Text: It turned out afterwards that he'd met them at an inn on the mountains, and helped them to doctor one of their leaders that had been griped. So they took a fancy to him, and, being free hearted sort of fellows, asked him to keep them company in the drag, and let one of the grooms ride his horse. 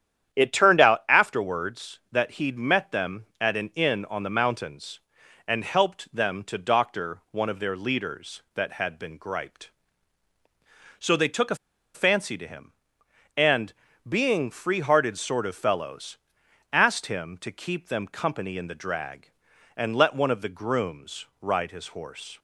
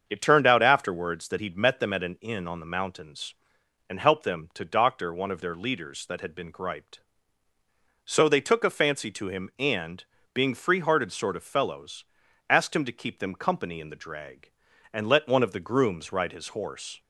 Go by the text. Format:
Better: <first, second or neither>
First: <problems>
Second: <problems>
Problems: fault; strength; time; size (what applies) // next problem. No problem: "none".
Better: second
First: starts louder than the rest; strong; until 1.4 s; 9.5 dB // pauses between "a" and "fancy"; at 11.5 s; 0.38 s long // pauses between "grooms" and "ride"; slight; at 21.2 s; 0.16 s long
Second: starts louder than the rest; until 1.1 s; 7 dB